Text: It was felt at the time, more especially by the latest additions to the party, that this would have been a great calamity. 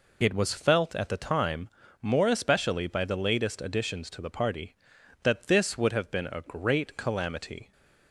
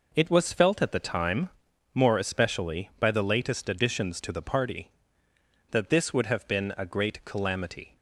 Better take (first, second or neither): neither